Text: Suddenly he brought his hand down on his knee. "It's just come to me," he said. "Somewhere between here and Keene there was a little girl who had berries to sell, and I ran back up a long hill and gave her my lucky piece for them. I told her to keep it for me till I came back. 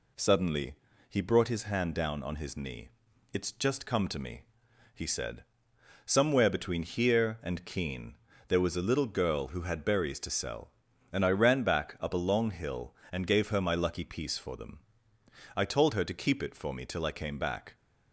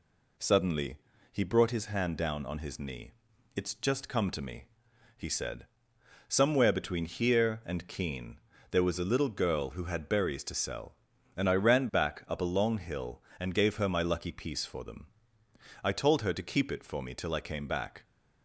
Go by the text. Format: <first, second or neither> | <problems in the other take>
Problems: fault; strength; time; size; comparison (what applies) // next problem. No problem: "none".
neither | pauses between "Suddenly" and "he"; slight; the same in both // pauses between "Keene" and "there"; slight; the same in both